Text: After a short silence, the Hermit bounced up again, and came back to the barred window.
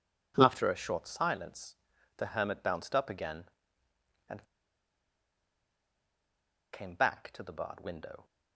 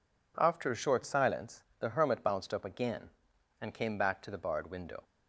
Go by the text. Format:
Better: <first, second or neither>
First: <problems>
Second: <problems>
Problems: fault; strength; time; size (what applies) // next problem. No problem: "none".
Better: second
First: pauses between "and" and "came"; strong; at 4.4 s; 2.2 s long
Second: none